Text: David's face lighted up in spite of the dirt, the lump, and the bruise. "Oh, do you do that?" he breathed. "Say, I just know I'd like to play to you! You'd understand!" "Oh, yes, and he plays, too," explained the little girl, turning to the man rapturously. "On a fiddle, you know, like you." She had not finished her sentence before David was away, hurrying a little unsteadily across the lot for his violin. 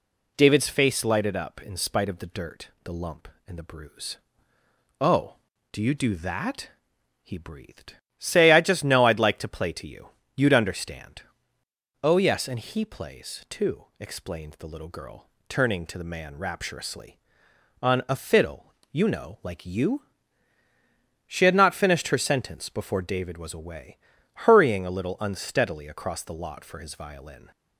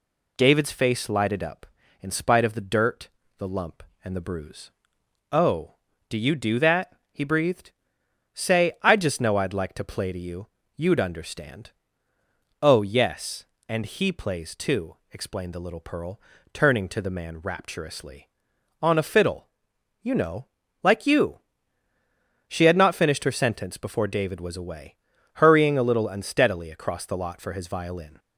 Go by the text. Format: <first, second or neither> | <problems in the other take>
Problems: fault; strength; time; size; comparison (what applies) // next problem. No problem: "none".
first | says "pearl" for "girl"; at 15.7 s